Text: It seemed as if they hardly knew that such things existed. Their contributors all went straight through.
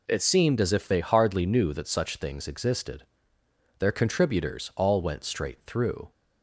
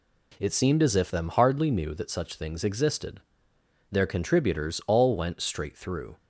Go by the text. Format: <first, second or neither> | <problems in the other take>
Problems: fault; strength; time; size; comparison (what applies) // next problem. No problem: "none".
first | says "them" for "they"; at 1.1 s